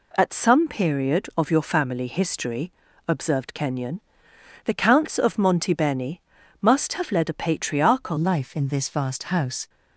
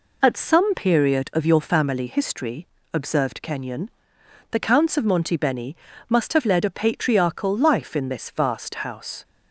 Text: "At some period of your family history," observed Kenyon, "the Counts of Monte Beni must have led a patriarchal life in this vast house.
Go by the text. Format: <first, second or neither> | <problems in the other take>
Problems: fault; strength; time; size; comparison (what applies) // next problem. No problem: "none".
second | pauses between "Beni" and "must"; at 6.1 s; 0.40 s long; slight in the second // changes voice at "life"; from 8.1 s on; 1.5 s long